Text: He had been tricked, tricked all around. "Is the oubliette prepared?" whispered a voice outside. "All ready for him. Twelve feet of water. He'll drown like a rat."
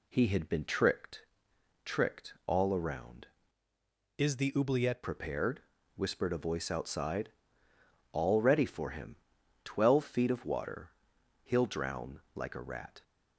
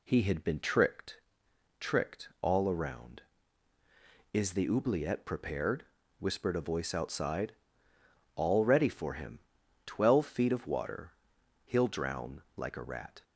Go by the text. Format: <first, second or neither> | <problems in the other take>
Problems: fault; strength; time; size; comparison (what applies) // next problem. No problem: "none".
second | changes voice from "Is" to "oubliette"; from 4.1 to 5.0 s; 0.9 s long